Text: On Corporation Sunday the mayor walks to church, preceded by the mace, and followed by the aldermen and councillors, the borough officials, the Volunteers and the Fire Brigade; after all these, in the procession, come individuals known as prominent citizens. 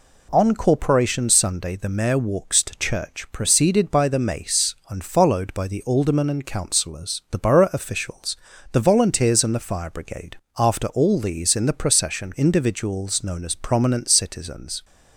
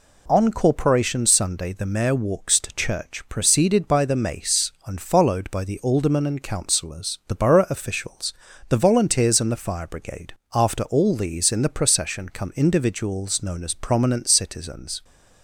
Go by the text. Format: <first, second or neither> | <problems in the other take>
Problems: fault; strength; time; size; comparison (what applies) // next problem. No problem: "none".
second | skips "come"; at 12.3 s